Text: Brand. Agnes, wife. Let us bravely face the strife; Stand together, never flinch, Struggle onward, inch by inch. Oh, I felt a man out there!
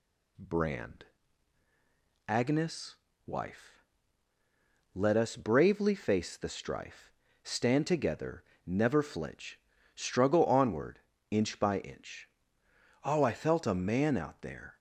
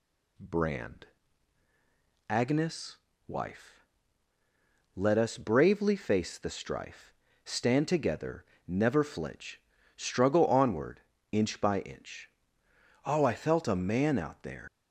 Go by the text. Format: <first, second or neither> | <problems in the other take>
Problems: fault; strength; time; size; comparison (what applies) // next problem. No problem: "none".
first | leaves "there" unfinished; at 14.6 s; 105 ms